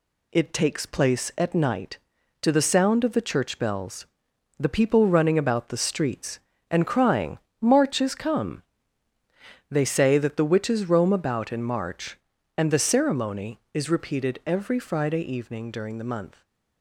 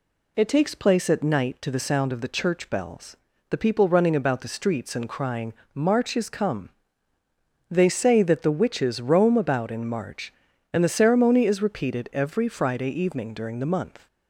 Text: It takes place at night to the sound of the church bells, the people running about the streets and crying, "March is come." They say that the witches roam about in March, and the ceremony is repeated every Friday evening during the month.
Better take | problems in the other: neither | none

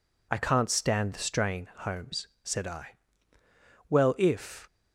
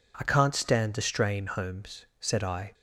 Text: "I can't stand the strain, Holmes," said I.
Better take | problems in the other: second | goes on to say "Well if"; noticeable; from 3.8 s on; 0.78 s long

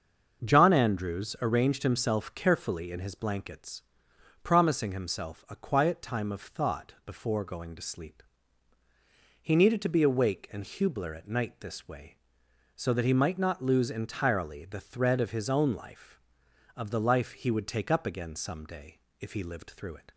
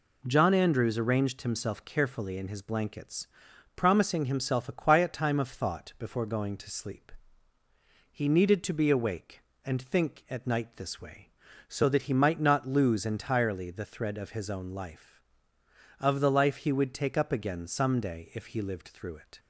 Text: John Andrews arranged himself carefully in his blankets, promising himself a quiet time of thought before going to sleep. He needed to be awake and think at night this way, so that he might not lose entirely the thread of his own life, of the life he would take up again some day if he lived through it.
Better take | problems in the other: second | starts louder than the rest; until 1.4 s; 6.5 dB // says "hubler" for "think"; at 10.6 s // pauses between "day" and "if"; slight; at 18.9 s; 0.20 s long

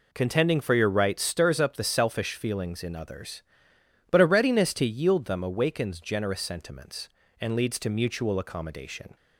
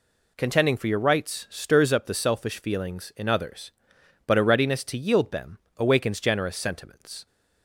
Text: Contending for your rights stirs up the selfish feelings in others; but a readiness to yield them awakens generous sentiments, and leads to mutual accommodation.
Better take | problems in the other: first | pauses between "them" and "awakens"; slight; at 5.5 s; 0.18 s long // stops before "and leads to mutual accommodation"; at 7.2 s

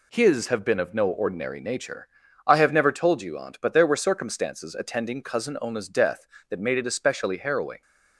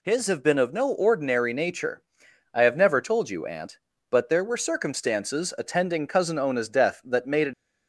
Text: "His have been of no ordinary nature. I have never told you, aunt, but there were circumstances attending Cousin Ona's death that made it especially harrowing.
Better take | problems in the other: first | stops before "especially harrowing"; at 7.5 s

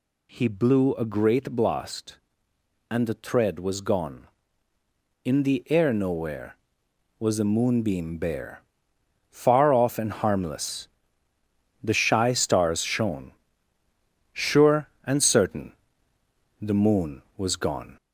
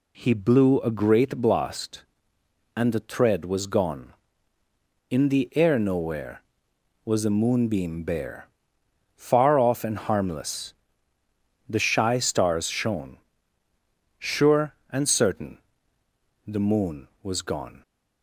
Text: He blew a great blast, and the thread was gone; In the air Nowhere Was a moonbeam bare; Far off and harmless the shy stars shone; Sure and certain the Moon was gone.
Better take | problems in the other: second | gets louder; slight; throughout; 2.5 dB // pauses between "harmless" and "the"; noticeable; at 10.8 s; 0.96 s long; noticeable in the second // pauses between "certain" and "the"; noticeable; at 15.7 s; 0.88 s long; noticeable in the second

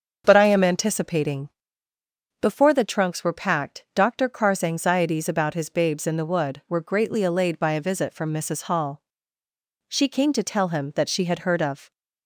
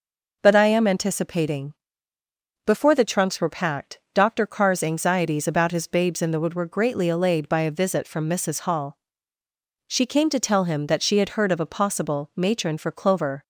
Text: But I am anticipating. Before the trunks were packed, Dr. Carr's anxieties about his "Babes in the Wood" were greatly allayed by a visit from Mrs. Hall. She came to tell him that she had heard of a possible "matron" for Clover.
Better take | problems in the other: second | starts louder than the rest; until 1.2 s; 7 dB // stops before "a possible matron for Clover"; at 11.9 s

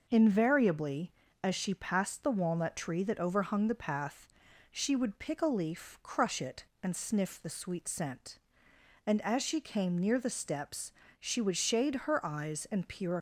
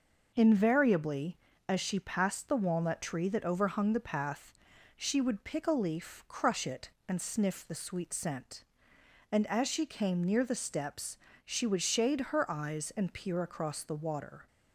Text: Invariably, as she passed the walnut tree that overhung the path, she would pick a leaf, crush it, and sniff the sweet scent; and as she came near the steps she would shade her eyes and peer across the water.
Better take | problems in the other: second | pauses between "steps" and "she"; slight; at 10.9 s; 0.26 s long; slight in the second // stops before "across the water"; at 13.1 s

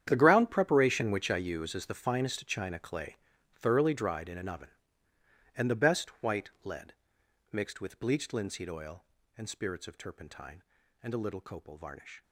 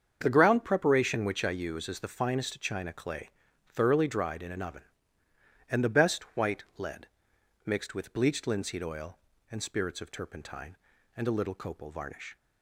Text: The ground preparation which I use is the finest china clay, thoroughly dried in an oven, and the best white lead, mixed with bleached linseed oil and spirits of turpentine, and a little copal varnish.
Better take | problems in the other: second | gets quieter; strong; throughout; 16 dB // starts louder than the rest; strong; until 1.0 s; 9.5 dB; strong in the second // pauses between "white" and "lead"; slight; at 6.4 s; 0.16 s long; slight in the second

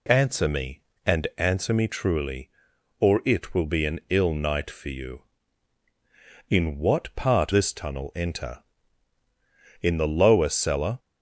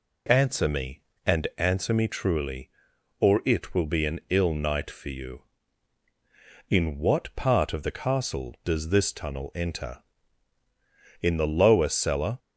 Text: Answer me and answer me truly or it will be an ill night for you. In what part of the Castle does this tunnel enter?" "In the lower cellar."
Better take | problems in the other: second | skips "of the Castle does"; at 7.5 s

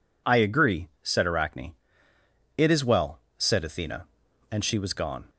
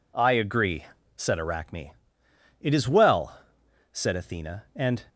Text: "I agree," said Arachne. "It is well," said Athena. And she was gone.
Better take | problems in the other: first | stops before "she was gone"; at 5.0 s

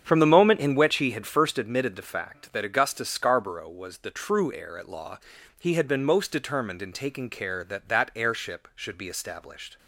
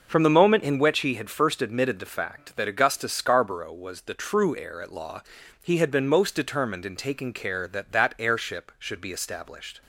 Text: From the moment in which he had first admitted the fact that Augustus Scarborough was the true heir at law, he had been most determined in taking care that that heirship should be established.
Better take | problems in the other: second | starts louder than the rest; strong; until 1.7 s; 8 dB

